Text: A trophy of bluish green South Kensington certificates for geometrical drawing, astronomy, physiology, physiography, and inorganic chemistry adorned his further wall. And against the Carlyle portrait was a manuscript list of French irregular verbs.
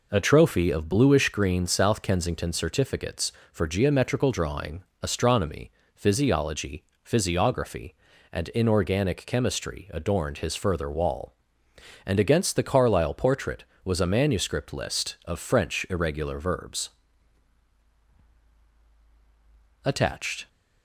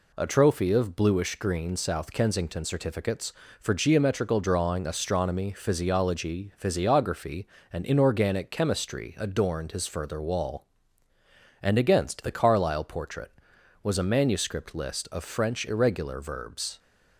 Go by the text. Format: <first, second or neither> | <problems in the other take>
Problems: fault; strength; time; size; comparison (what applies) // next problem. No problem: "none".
second | goes on to say "Attached"; noticeable; from 19.8 s on; 0.64 s long